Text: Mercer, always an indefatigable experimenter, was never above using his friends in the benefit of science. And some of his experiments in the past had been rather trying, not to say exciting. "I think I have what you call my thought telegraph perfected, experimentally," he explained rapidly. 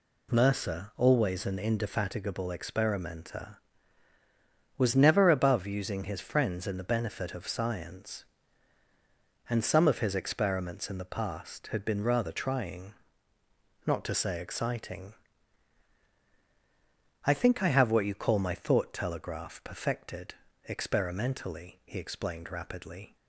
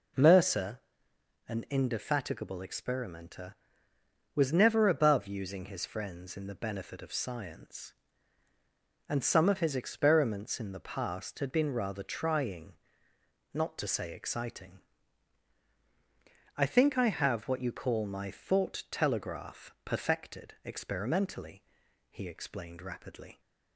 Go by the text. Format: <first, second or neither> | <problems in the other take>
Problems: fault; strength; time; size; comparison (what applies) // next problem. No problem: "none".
first | skips "always"; at 1.1 s